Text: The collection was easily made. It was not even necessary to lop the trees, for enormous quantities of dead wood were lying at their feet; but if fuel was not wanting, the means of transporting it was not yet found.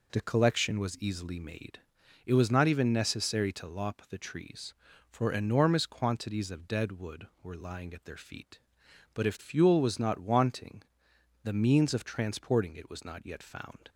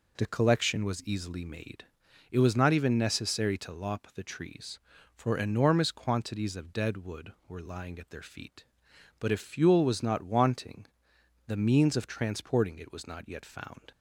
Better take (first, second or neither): neither